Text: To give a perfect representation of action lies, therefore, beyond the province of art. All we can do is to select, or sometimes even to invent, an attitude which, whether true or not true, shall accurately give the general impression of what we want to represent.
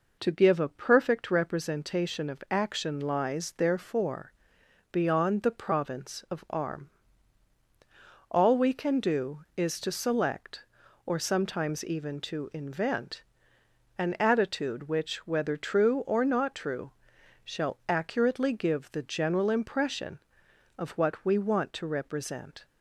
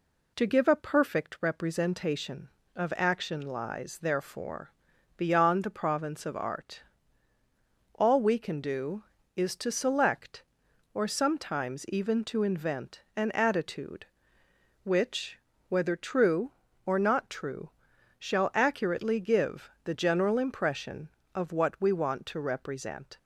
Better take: second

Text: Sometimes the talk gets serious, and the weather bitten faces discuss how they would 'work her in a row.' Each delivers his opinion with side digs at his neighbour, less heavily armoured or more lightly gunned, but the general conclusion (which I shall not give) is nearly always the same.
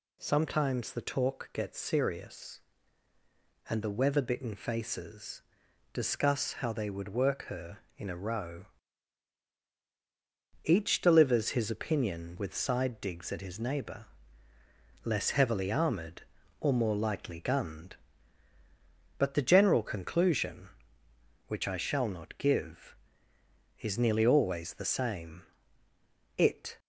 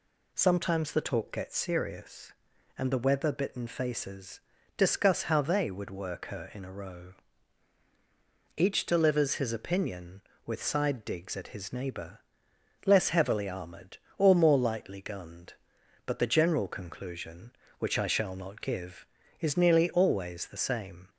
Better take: second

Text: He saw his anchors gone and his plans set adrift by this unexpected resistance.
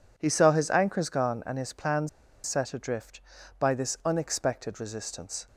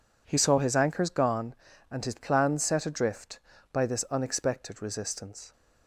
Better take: second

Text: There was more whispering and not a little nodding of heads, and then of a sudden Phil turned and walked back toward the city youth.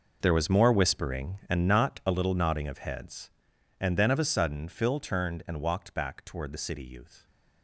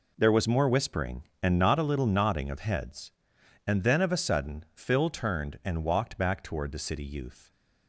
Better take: second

